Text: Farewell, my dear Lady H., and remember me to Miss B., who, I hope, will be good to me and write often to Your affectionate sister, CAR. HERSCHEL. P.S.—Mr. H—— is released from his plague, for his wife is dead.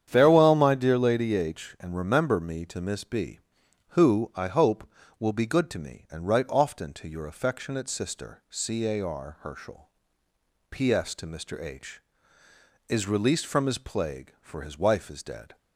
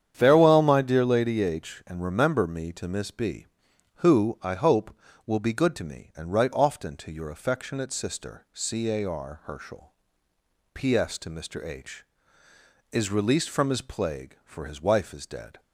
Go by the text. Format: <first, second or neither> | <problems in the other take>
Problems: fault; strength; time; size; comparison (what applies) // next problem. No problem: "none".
neither | starts louder than the rest; strong; the same in both